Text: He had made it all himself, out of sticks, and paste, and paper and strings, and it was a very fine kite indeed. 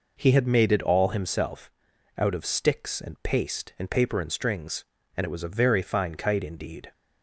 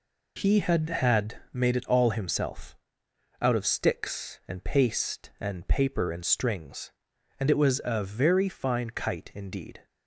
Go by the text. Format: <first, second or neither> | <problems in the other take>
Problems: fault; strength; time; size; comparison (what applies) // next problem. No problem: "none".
first | says "had" twice; at 0.8 s